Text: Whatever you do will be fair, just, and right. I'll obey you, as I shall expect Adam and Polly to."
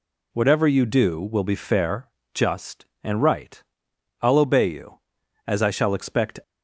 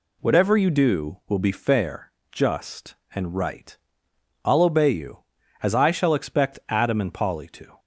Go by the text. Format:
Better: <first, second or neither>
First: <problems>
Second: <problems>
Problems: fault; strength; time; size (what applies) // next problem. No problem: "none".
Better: second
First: stops before "Adam and Polly to"; at 6.4 s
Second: none